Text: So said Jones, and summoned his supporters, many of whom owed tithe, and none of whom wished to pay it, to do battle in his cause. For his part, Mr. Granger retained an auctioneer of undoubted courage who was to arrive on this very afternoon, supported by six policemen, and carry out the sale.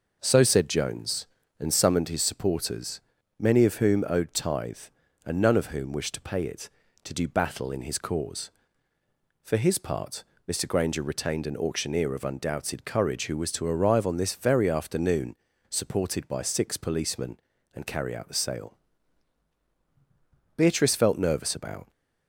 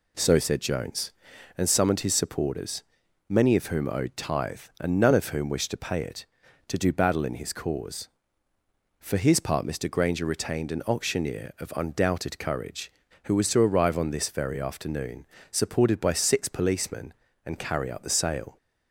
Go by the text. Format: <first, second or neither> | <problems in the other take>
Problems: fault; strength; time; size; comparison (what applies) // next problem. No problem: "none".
second | goes on to say "Beatrice felt nervous about"; from 20.5 s on; 1.3 s long